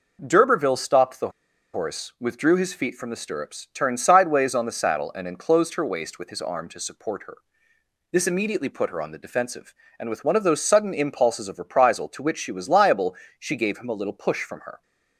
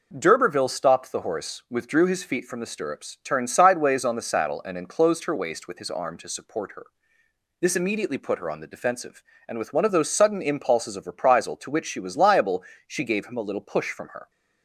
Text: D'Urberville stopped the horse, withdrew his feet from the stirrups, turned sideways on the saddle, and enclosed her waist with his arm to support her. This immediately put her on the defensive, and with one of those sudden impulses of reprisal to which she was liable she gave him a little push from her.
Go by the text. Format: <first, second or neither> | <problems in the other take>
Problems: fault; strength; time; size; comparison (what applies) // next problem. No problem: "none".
second | pauses between "the" and "horse"; at 1.2 s; 0.43 s long // pauses between "liable" and "she"; slight; at 13.1 s; 0.24 s long; slight in the second